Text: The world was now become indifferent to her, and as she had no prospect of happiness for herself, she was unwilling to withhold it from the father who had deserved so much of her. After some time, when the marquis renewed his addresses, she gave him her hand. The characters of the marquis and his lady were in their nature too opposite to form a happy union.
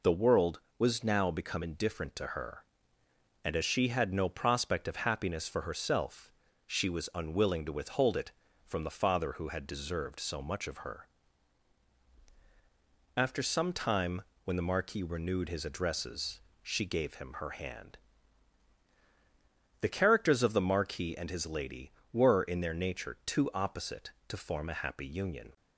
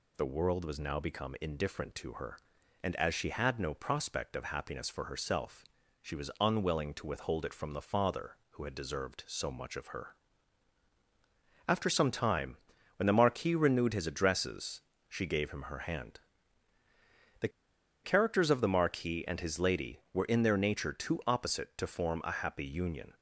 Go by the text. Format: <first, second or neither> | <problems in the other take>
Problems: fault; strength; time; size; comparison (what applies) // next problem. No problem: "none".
first | pauses between "The" and "characters"; noticeable; at 17.4 s; 0.55 s long